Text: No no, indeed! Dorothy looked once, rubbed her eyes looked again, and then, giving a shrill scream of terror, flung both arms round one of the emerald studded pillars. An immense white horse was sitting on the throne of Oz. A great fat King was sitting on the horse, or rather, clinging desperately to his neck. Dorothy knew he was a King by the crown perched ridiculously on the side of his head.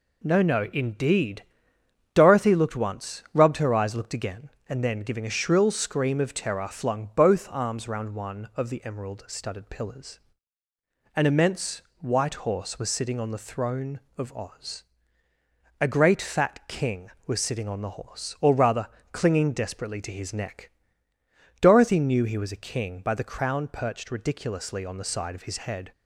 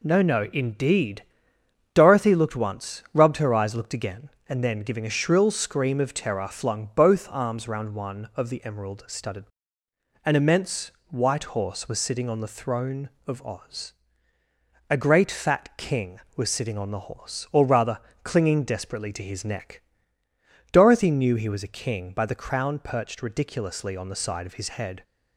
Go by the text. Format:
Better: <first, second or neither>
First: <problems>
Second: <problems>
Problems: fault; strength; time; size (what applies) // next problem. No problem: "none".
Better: first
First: pauses between "immense" and "white"; slight; at 11.8 s; 0.18 s long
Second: skips "pillars"; at 9.8 s // pauses between "immense" and "white"; slight; at 10.9 s; 0.18 s long